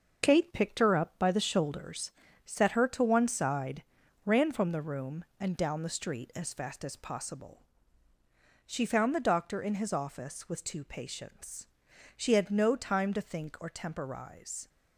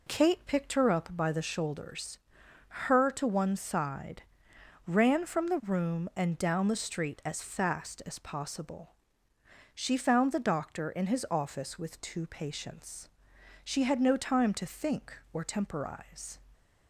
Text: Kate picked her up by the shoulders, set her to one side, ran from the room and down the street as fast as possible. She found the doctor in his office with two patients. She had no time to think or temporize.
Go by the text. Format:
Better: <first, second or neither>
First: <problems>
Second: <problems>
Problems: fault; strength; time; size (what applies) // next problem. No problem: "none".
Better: first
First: none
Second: skips "set"; at 2.4 s